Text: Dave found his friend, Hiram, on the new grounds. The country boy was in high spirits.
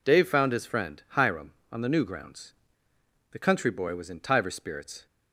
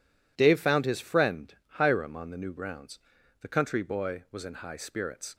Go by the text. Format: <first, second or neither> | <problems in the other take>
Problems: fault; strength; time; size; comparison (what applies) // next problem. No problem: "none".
second | says "tiver" for "high"; at 4.1 s